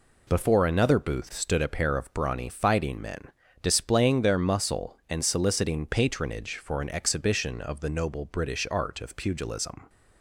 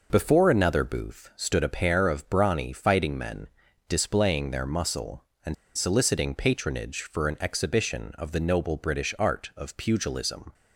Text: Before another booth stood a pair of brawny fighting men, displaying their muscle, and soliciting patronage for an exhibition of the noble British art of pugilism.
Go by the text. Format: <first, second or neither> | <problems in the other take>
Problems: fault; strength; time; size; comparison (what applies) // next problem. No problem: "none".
first | pauses between "and" and "soliciting"; slight; at 5.5 s; 0.22 s long